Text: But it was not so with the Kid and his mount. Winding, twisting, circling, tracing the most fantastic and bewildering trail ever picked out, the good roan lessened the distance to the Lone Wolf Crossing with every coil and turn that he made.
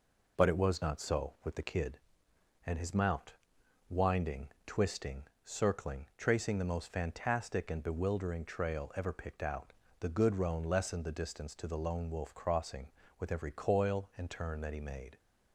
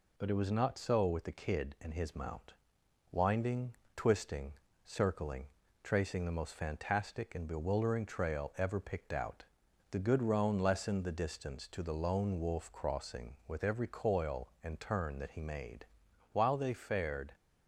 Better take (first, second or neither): first